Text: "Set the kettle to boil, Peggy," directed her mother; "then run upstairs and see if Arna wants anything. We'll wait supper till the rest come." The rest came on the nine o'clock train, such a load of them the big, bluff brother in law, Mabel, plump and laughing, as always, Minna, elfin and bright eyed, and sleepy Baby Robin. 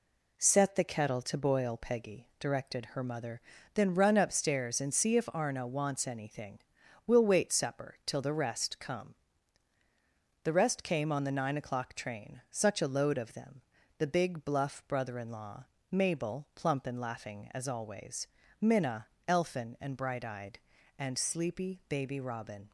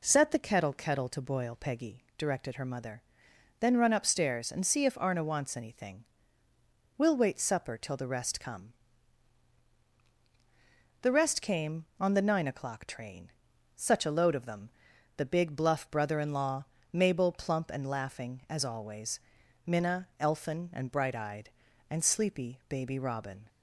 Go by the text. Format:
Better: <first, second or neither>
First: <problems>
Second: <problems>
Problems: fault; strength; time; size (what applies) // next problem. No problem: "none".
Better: first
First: pauses between "them" and "the"; slight; at 13.6 s; 0.36 s long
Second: says "kettle" twice; at 0.7 s // pauses between "them" and "the"; at 14.7 s; 0.44 s long